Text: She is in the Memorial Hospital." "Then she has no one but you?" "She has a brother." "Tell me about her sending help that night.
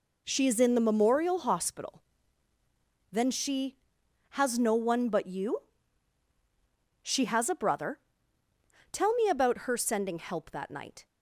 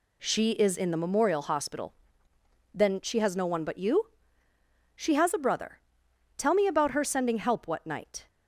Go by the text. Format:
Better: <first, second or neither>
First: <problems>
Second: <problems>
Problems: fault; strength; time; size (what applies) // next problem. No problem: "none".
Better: first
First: none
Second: says "what" for "that"; at 7.6 s